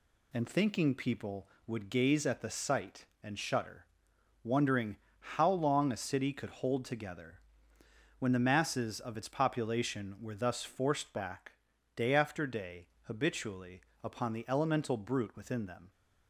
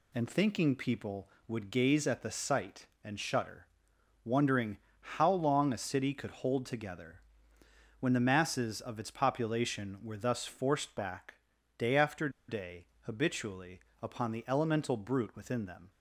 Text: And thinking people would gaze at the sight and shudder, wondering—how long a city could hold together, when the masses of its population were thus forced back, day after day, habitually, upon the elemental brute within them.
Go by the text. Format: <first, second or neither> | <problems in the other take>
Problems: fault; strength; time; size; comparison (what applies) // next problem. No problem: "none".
first | pauses between "after" and "day"; slight; at 12.2 s; 0.19 s long